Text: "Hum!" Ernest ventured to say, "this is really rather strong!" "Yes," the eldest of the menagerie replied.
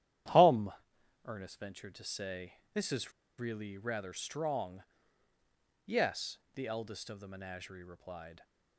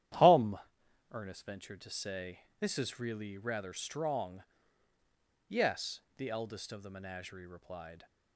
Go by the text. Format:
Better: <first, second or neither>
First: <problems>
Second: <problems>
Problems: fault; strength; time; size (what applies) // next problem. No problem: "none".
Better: second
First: starts louder than the rest; strong; until 1.8 s; 11 dB // pauses between "is" and "really"; slight; at 3.1 s; 0.27 s long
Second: starts louder than the rest; strong; until 1.6 s; 11 dB